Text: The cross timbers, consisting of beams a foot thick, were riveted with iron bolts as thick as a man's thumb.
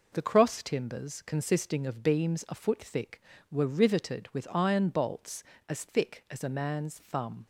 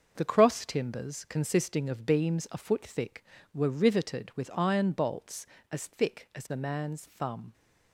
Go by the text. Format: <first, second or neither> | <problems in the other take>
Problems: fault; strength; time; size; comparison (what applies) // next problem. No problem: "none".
first | gets quieter; strong; throughout; 8 dB